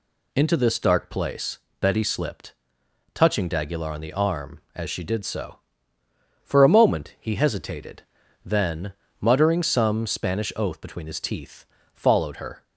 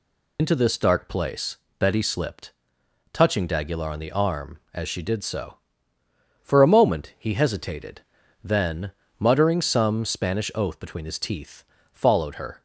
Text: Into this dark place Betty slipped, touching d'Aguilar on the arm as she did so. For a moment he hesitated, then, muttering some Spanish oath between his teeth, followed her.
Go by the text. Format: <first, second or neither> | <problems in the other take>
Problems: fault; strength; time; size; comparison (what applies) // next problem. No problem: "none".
first | loses the start of "Into"; at 0.3 s; 80 ms // pauses between "place" and "Betty"; slight; at 1.5 s; 0.22 s long; slight in the first